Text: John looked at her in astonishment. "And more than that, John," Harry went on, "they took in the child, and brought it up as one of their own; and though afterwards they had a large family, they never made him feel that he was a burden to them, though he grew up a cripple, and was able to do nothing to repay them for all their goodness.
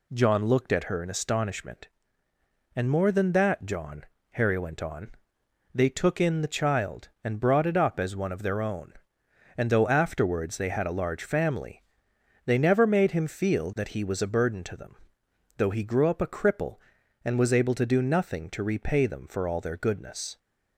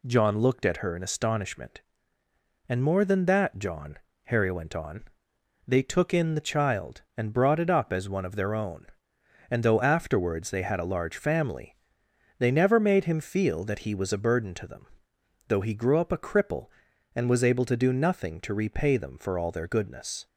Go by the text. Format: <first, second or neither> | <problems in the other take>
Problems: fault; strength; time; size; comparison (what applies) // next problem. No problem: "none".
neither | none